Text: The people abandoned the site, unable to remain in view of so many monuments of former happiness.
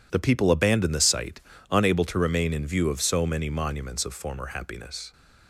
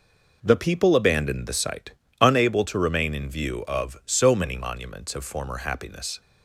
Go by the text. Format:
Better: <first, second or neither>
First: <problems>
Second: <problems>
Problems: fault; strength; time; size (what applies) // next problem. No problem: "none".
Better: neither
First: none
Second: none